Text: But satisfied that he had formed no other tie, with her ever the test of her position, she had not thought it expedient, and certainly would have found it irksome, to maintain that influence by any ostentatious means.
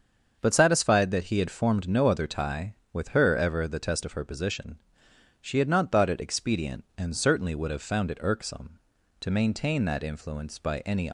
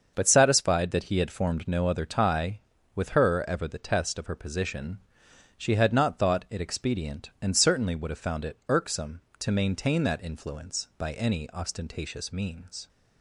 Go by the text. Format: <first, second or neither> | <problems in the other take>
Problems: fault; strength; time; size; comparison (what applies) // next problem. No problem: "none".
second | starts louder than the rest; until 1.4 s; 7 dB; also in the second // stops before "ostentatious means"; at 11.0 s